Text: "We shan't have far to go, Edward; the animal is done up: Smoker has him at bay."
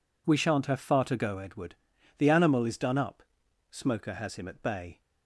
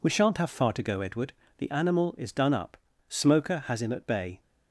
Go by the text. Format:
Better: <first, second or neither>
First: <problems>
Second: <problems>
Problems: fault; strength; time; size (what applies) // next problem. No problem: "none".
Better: neither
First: none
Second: none